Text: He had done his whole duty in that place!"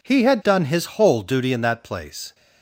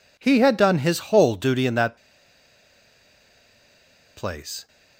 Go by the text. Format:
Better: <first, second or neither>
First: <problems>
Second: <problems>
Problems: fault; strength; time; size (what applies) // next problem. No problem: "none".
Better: first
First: none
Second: pauses between "that" and "place"; strong; at 1.9 s; 2.2 s long